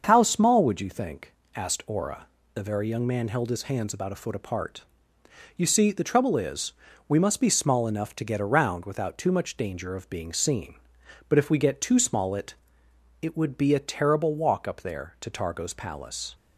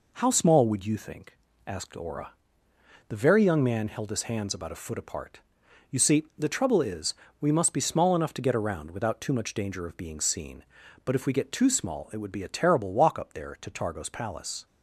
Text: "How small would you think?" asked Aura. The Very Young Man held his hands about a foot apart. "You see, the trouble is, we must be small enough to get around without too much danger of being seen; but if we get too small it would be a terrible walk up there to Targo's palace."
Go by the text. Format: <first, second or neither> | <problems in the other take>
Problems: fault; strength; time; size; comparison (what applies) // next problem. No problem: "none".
second | starts louder than the rest; until 1.0 s; 6.5 dB // says "it" twice; at 13.2 s